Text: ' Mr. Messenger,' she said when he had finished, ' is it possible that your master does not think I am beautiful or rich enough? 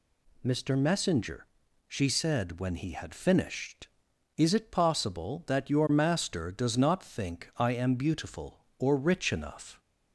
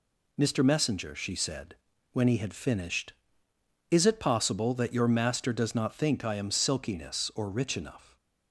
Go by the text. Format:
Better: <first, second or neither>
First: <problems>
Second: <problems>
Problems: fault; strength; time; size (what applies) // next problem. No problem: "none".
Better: first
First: none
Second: pauses between "said" and "when"; at 1.7 s; 0.38 s long // says "silkiness" for "beautiful"; at 6.5 s